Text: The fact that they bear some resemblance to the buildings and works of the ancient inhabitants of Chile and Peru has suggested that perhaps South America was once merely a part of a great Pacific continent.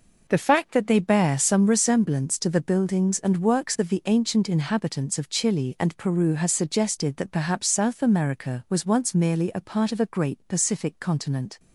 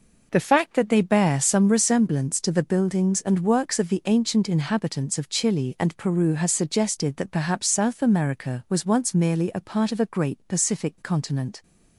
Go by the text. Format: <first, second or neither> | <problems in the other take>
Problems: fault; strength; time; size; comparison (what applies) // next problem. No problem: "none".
neither | none